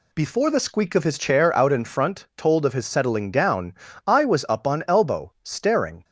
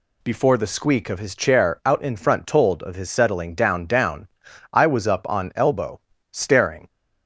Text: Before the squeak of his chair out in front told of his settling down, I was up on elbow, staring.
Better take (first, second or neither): first